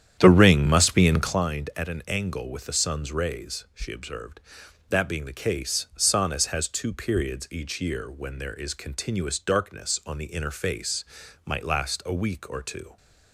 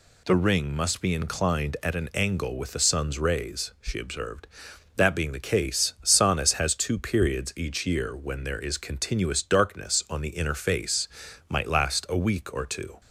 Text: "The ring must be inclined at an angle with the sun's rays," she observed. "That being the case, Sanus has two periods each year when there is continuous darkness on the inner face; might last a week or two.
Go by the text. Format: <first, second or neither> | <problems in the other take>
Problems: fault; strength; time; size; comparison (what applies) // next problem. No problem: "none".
second | starts louder than the rest; strong; until 1.5 s; 9.5 dB